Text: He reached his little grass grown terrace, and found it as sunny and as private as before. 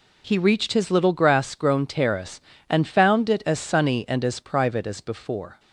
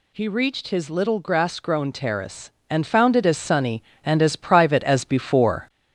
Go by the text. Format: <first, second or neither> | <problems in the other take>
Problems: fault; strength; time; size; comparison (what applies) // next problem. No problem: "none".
first | gets louder; slight; throughout; 2.5 dB